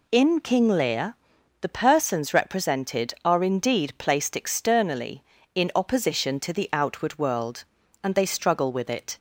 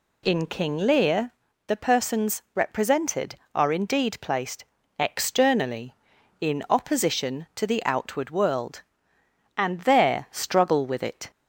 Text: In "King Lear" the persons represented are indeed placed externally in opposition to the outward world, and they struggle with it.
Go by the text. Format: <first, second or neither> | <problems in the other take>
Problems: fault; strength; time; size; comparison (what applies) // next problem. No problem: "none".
first | pauses between "Lear" and "the"; slight; at 1.3 s; 0.34 s long; also in the first // pauses between "placed" and "externally"; slight; at 4.6 s; 0.34 s long // says "there" for "they"; at 9.8 s